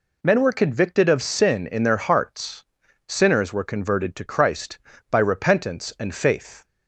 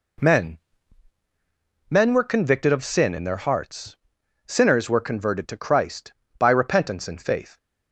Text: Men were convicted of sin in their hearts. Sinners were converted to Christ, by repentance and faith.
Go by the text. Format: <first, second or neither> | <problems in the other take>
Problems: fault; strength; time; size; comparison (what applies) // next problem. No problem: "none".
first | says "Men" twice; at 1.8 s